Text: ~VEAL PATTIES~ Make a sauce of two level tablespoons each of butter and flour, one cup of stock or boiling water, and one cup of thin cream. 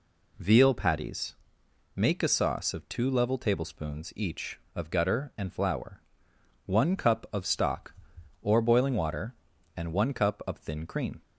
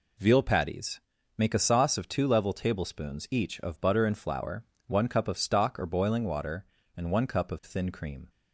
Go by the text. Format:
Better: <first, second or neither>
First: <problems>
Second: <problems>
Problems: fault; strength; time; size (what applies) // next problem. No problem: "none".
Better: second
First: says "gutter" for "butter"; at 4.8 s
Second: none